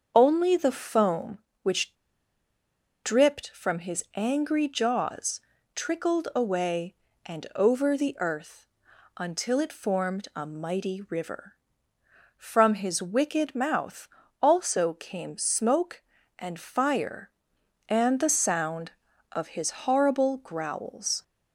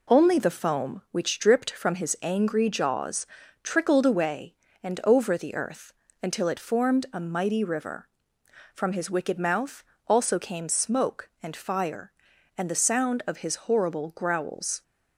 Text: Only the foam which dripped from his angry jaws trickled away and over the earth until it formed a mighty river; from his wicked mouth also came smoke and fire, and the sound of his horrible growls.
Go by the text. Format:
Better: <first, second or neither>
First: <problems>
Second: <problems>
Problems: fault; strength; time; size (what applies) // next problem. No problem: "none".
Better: second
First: starts louder than the rest; until 1.1 s; 6.5 dB // pauses between "which" and "dripped"; at 1.9 s; 1.0 s long // pauses between "jaws" and "trickled"; slight; at 5.4 s; 0.34 s long // pauses between "earth" and "until"; noticeable; at 8.6 s; 0.50 s long // pauses between "mouth" and "also"; slight; at 14.0 s; 0.36 s long // pauses between "his" and "horrible"; slight; at 19.7 s; 0.16 s long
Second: pauses between "jaws" and "trickled"; at 3.2 s; 0.38 s long // pauses between "earth" and "until"; slight; at 5.9 s; 0.30 s long // pauses between "mouth" and "also"; slight; at 9.8 s; 0.24 s long